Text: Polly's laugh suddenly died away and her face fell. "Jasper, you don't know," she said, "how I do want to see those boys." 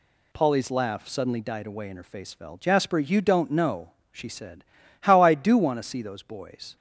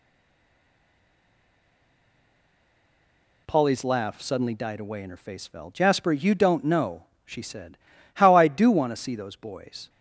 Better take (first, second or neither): first